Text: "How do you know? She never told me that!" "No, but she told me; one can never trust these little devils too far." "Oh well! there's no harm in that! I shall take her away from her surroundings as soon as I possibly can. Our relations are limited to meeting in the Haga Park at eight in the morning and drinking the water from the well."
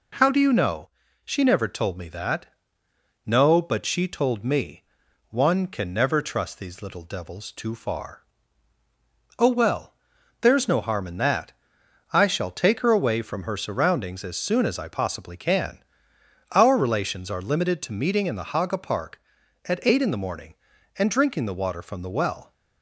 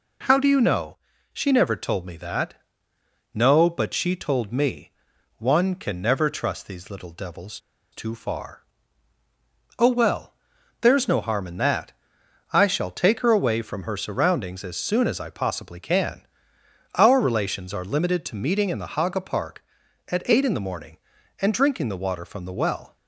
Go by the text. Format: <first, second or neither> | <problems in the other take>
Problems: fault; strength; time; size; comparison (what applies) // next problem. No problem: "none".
first | pauses between "devils" and "too"; slight; at 7.5 s; 0.34 s long